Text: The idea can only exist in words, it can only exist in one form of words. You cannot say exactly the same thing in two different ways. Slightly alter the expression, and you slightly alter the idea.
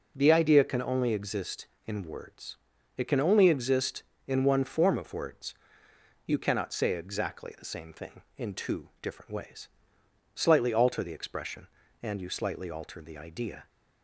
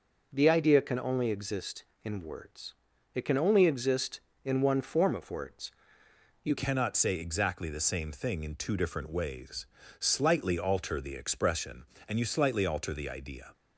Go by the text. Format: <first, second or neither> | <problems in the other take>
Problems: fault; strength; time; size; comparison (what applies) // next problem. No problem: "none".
first | changes voice at "cannot"; from 6.5 s on; 7.0 s long